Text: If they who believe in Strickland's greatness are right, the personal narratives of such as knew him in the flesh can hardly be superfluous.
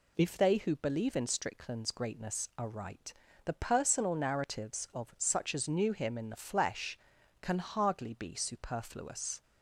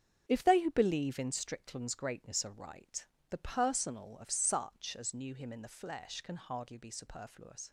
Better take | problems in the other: first | starts louder than the rest; strong; until 1.2 s; 7.5 dB // skips "narratives"; at 4.1 s

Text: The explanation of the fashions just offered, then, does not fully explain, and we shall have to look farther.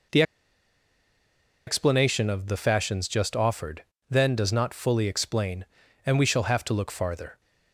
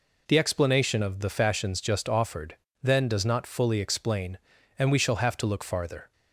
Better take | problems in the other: second | pauses between "The" and "explanation"; strong; at 0.2 s; 1.4 s long

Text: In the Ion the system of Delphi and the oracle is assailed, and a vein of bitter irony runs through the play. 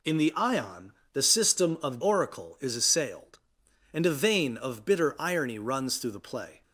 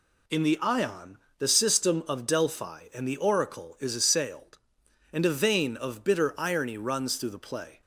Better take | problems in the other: second | pauses between "Ion" and "the"; slight; at 0.9 s; 0.20 s long; slight in the second // skips "Delphi and the"; at 2.0 s

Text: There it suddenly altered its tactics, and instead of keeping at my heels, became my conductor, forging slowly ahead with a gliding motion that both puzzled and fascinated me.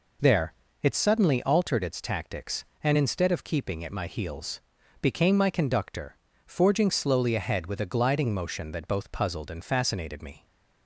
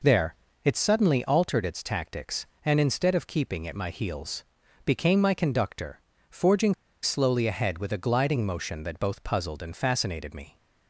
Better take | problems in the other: first | pauses between "There" and "it"; slight; at 0.3 s; 0.30 s long; slight in the first // pauses between "forging" and "slowly"; slight; at 6.7 s; 0.28 s long

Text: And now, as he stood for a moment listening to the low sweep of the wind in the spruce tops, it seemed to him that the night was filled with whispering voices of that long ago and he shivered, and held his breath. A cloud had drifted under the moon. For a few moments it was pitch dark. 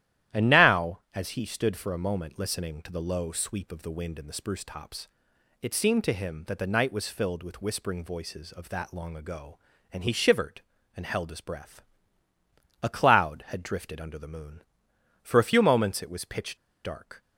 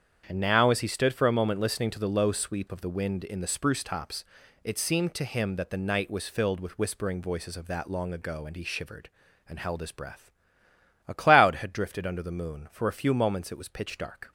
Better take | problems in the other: second | starts louder than the rest; strong; until 1.4 s; 12.5 dB; strong in the second // pauses between "pitch" and "dark"; slight; at 16.5 s; 0.27 s long

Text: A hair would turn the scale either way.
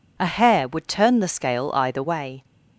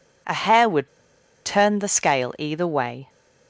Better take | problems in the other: first | pauses between "would" and "turn"; noticeable; at 0.8 s; 0.57 s long

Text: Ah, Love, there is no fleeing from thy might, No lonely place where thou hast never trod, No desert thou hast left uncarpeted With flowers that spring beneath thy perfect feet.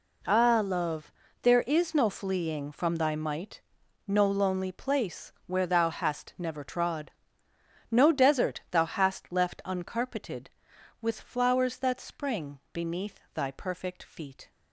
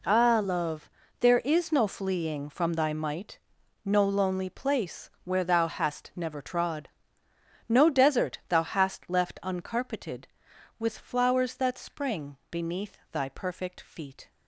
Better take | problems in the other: neither | pauses between "beneath" and "thy"; slight; the same in both

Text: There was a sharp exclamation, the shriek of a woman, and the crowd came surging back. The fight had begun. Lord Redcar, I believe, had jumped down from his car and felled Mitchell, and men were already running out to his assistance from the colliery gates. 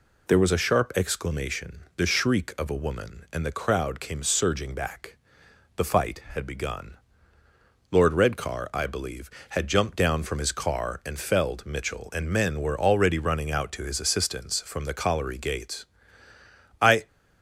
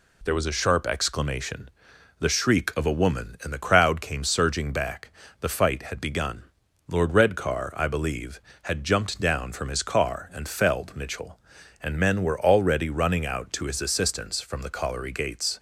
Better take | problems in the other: second | goes on to say "I"; slight; from 16.8 s on; 0.26 s long

